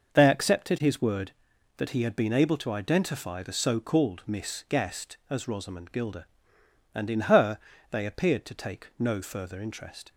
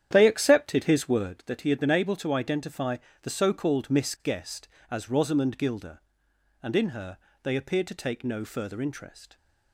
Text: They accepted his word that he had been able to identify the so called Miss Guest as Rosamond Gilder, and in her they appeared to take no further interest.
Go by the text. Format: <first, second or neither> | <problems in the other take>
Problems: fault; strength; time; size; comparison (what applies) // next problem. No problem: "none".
first | starts louder than the rest; strong; until 1.5 s; 9.5 dB // pauses between "identify" and "the"; slight; at 2.9 s; 0.24 s long // pauses between "her" and "they"; slight; at 7.1 s; 0.24 s long; slight in the first